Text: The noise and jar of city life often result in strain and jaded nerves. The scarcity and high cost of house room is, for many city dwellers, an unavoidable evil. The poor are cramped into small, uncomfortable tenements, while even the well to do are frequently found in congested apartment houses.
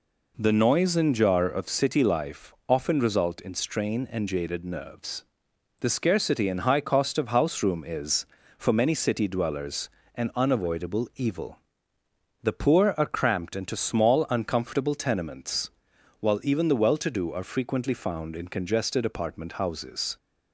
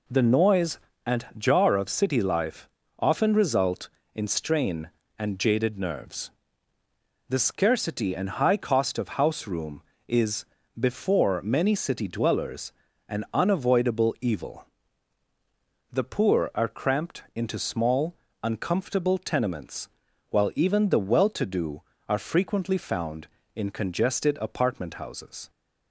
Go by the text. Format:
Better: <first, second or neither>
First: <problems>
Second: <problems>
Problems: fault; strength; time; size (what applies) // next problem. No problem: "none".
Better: first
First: pauses between "life" and "often"; slight; at 2.5 s; 0.16 s long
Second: pauses between "life" and "often"; slight; at 2.6 s; 0.32 s long // says "before" for "for"; at 10.7 s